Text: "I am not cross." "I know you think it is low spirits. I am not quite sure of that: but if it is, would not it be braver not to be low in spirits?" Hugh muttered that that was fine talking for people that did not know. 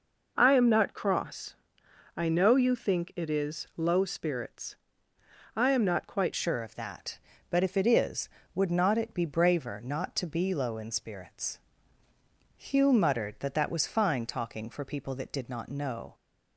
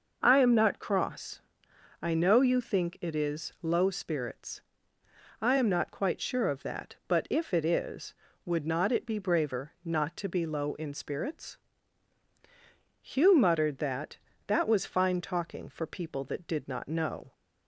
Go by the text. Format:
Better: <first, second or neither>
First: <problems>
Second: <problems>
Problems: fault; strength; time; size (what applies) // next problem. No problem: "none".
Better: second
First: changes voice at "sure"; from 6.3 s on; 9.8 s long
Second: none